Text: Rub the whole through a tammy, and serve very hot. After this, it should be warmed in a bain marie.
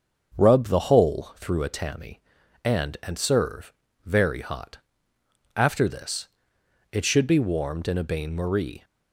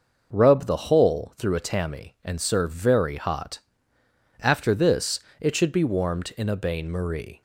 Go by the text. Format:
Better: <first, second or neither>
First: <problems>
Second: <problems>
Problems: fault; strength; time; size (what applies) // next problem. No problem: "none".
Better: second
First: starts louder than the rest; until 1.4 s; 7 dB // says "and" twice; at 3.0 s // pauses between "serve" and "very"; slight; at 3.7 s; 0.32 s long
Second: none